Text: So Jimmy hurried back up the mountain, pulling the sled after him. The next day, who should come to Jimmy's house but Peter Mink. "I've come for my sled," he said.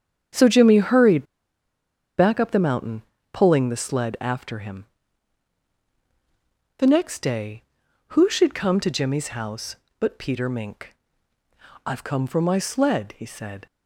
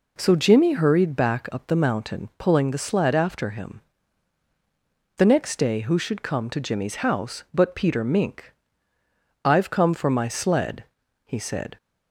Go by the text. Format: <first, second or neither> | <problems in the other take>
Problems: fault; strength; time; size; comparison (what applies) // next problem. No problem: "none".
second | starts louder than the rest; strong; until 2.2 s; 8 dB // pauses between "hurried" and "back"; noticeable; at 1.2 s; 0.94 s long